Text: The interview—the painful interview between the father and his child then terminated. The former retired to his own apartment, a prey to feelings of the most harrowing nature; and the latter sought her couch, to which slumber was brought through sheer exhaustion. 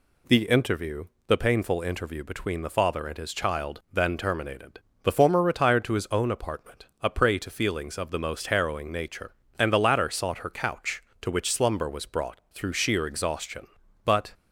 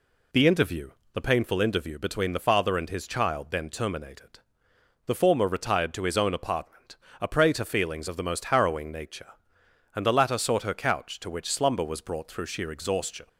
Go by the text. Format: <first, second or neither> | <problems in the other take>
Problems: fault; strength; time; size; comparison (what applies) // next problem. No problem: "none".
second | goes on to say "But"; slight; from 14.0 s on; 0.26 s long